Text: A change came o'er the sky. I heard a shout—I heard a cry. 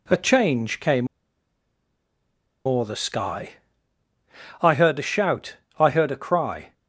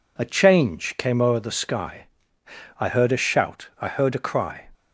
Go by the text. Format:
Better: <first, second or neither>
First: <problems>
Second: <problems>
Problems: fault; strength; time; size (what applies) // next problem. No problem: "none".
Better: second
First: pauses between "came" and "o'er"; strong; at 1.0 s; 1.5 s long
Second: none